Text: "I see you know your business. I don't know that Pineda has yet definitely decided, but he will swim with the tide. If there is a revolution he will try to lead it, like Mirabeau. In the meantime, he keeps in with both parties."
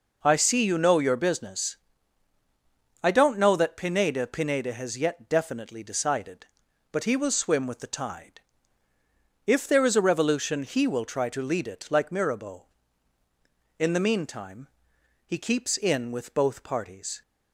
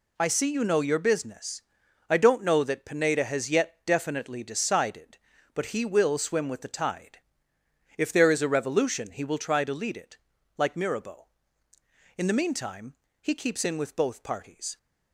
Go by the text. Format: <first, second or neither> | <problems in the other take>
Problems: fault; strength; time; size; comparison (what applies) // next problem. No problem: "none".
second | says "Pineda" twice; at 4.2 s